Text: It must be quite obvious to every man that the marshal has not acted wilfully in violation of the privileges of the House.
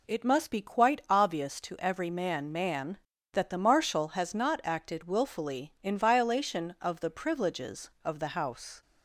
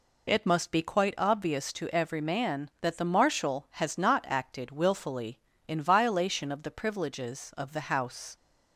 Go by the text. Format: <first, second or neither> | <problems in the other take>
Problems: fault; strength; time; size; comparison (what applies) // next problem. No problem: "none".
second | says "man" twice; at 2.5 s